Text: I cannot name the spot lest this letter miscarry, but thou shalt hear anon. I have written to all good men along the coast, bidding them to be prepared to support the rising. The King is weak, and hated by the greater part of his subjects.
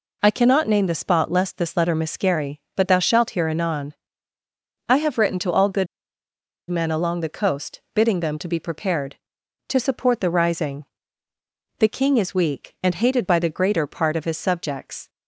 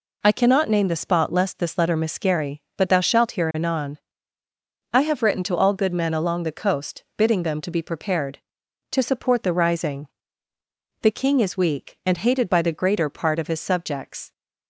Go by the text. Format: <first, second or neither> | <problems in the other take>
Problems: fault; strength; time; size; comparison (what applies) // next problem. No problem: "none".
second | pauses between "good" and "men"; noticeable; at 5.8 s; 0.82 s long